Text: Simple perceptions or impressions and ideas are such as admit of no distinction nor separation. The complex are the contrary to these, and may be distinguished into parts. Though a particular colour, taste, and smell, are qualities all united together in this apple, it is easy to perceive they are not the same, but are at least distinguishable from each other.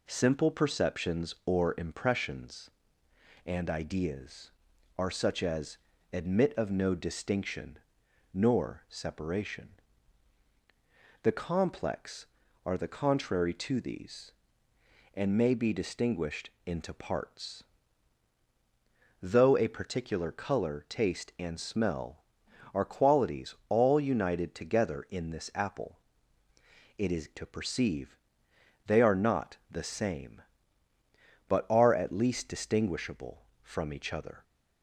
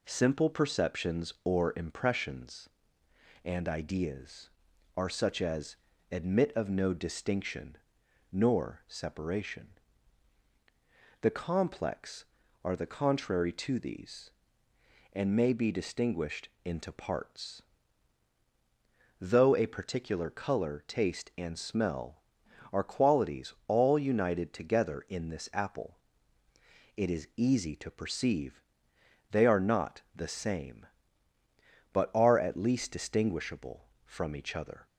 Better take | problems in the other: second | pauses between "as" and "admit"; slight; at 5.7 s; 0.34 s long; slight in the second // pauses between "distinction" and "nor"; noticeable; at 7.7 s; 0.56 s long; noticeable in the second // skips "easy"; at 27.3 s // pauses between "perceive" and "they"; noticeable; at 28.1 s; 0.70 s long; noticeable in the second

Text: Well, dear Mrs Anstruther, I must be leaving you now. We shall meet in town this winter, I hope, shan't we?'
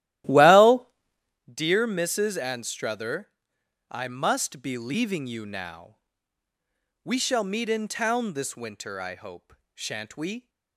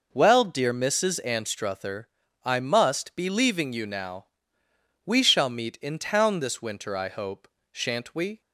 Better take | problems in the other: second | starts louder than the rest; strong; until 1.5 s; 14.5 dB

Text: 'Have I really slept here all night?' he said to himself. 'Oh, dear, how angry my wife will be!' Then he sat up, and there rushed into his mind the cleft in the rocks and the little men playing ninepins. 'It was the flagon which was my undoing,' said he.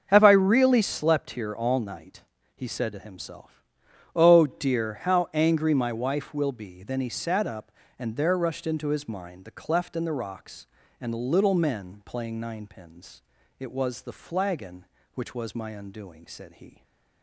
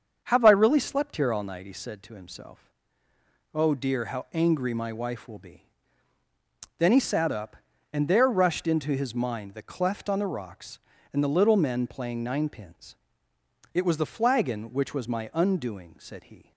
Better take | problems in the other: first | starts louder than the rest; until 1.2 s; 7 dB; also in the first // says "on" for "in"; at 10.0 s

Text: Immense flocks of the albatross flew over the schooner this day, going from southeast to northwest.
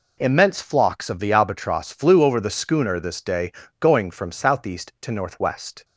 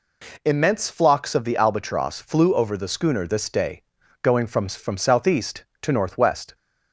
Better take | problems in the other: first | says "from" twice; at 4.6 s

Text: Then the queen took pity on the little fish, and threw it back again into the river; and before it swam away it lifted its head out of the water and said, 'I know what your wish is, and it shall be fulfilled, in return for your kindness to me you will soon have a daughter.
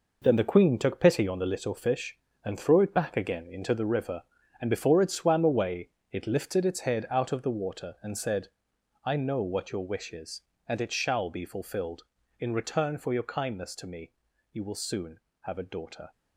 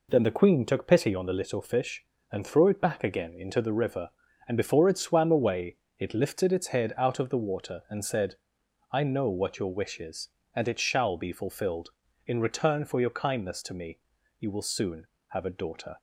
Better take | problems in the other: second | gets quieter; strong; throughout; 9.5 dB // pauses between "away" and "it"; slight; at 5.8 s; 0.24 s long; slight in the second // pauses between "me" and "you"; at 14.1 s; 0.40 s long; also in the second

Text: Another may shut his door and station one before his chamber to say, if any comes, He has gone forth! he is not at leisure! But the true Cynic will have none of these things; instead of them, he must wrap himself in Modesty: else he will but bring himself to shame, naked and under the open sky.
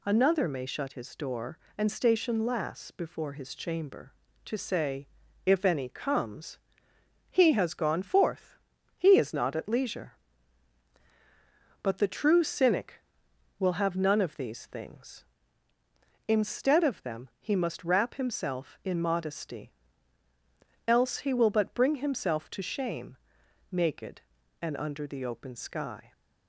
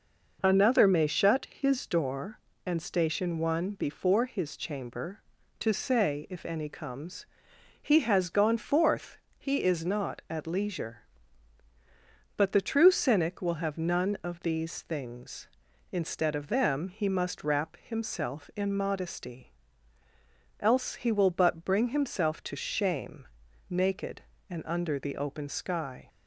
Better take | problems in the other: second | says "lass" for "one"; at 2.4 s

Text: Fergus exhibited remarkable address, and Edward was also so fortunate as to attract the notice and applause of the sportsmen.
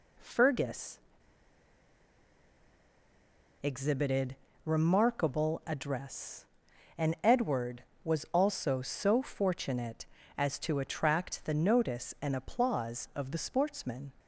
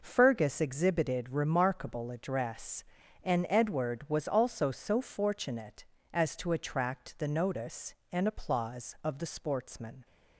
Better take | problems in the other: second | pauses between "Fergus" and "exhibited"; strong; at 0.9 s; 2.6 s long // pauses between "exhibited" and "remarkable"; slight; at 4.3 s; 0.30 s long

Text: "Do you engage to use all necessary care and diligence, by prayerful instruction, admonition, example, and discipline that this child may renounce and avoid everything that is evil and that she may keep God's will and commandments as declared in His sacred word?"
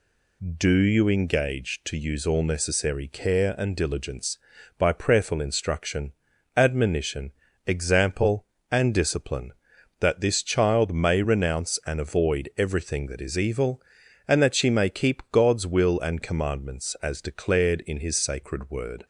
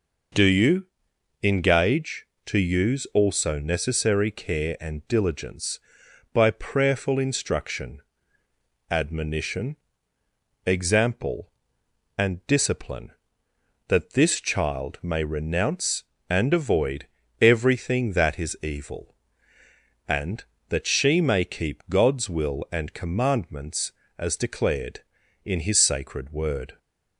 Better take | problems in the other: first | pauses between "you" and "engage"; noticeable; at 0.8 s; 0.56 s long // says "also" for "all"; at 3.1 s // pauses between "avoid" and "everything"; slight; at 17.0 s; 0.36 s long

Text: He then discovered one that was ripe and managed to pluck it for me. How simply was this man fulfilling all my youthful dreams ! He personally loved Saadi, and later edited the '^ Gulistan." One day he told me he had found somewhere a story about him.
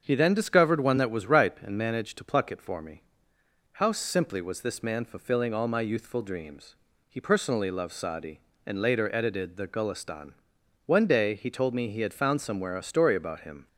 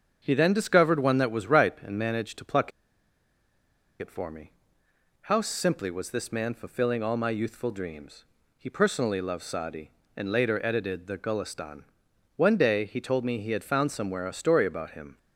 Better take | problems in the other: first | starts louder than the rest; until 1.2 s; 6.5 dB; also in the first // pauses between "pluck" and "it"; strong; at 2.7 s; 1.2 s long

